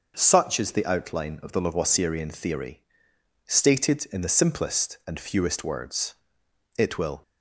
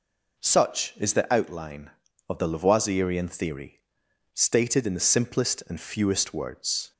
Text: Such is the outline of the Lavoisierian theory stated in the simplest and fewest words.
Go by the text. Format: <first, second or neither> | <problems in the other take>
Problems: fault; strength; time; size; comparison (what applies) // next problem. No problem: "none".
second | pauses between "theory" and "stated"; noticeable; at 2.7 s; 0.68 s long; noticeable in the second // goes on to say "It will"; slight; from 6.7 s on; 0.44 s long